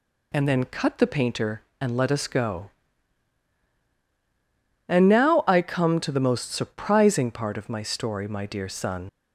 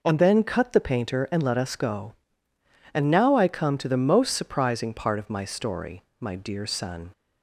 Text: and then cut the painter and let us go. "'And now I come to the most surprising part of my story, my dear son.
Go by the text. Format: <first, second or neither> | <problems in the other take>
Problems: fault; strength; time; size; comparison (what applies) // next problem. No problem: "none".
second | leaves "son" unfinished; at 9.0 s; 75 ms